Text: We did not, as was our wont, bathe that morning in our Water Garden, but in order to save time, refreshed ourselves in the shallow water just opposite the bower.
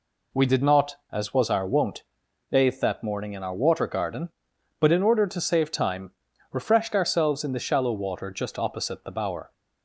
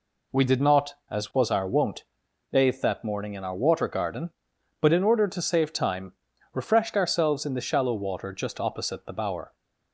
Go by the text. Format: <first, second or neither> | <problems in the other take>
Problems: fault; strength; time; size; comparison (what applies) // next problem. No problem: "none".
neither | none